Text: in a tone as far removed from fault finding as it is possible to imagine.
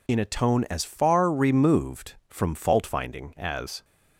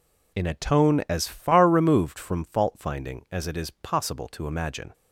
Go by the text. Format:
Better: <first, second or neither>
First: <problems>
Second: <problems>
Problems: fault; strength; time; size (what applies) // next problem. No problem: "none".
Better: second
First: stops before "it is possible to imagine"; at 3.8 s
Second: none